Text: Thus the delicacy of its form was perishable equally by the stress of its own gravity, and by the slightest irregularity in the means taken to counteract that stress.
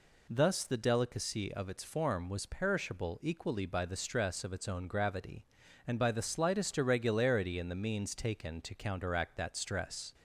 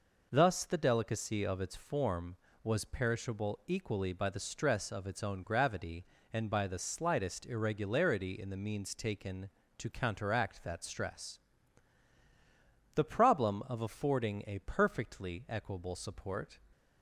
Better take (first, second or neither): first